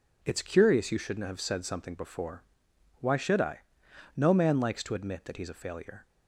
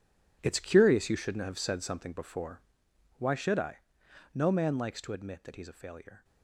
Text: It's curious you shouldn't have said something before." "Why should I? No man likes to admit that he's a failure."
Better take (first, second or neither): first